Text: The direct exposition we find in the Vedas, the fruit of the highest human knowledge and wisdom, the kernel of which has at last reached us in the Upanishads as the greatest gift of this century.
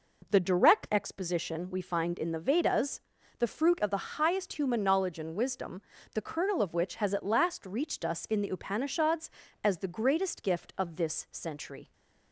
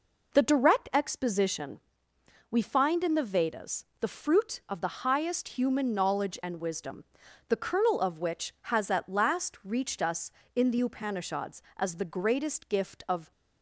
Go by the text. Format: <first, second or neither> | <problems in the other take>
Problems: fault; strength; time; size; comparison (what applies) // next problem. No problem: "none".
first | pauses between "exposition" and "we"; noticeable; at 1.7 s; 0.70 s long // stops before "this century"; at 13.3 s